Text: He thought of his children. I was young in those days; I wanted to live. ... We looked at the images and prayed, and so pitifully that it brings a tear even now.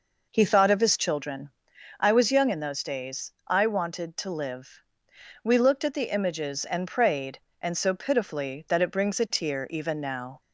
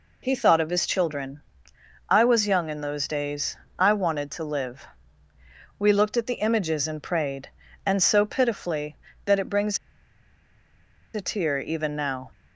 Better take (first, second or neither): first